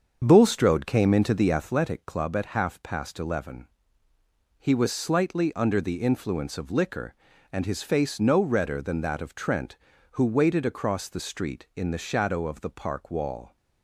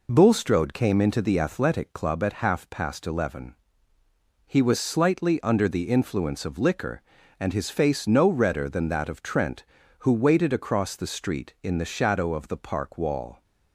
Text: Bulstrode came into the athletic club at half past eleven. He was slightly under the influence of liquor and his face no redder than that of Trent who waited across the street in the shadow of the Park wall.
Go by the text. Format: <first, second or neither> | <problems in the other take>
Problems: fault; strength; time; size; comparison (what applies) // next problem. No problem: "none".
second | starts louder than the rest; until 1.7 s; 7 dB